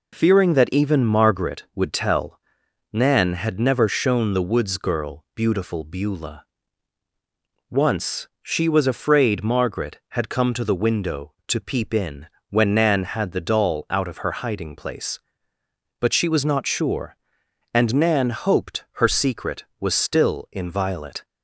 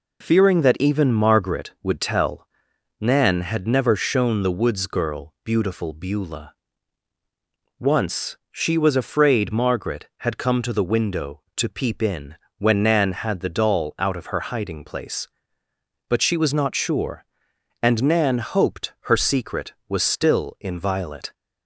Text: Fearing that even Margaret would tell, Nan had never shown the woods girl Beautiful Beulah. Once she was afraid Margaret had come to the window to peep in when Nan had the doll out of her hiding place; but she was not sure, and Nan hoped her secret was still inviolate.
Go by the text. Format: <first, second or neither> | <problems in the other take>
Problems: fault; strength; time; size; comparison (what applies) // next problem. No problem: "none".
neither | pauses between "in" and "when"; slight; the same in both